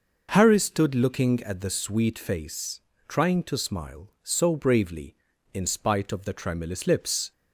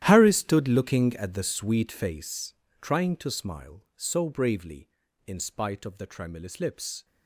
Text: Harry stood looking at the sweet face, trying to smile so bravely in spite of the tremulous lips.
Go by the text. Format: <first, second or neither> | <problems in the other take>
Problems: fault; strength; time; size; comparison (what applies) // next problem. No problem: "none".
first | gets quieter; strong; throughout; 16 dB